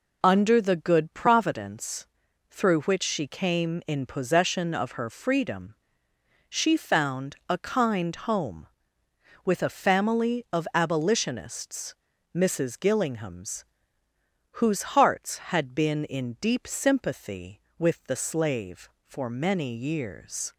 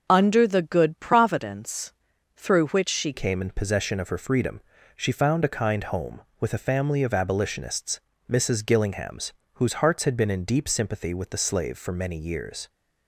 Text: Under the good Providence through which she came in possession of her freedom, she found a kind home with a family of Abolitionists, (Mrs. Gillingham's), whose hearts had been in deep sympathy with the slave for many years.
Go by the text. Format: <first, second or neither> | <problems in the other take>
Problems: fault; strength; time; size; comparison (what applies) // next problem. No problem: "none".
first | pauses between "Providence" and "through"; at 1.9 s; 0.44 s long; also in the first // changes voice at "came"; from 3.1 s on; 9.5 s long